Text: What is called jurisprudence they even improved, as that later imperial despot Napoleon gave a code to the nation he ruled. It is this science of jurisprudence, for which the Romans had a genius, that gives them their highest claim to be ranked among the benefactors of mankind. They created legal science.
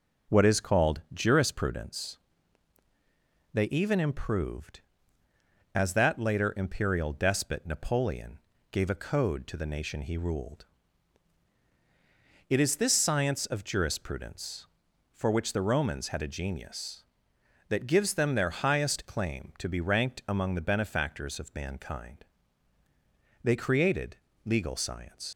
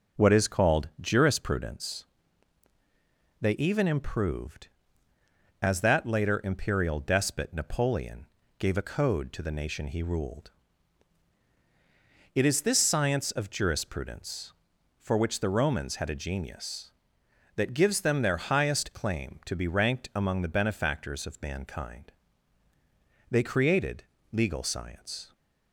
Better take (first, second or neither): second